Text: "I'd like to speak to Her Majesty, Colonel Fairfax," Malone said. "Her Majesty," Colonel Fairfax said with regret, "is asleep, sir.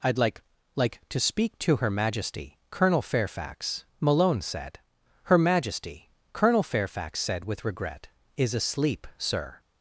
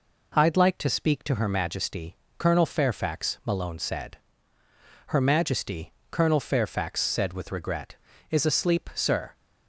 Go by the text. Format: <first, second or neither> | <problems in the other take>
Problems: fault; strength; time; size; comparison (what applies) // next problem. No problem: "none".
second | says "like" twice; at 0.7 s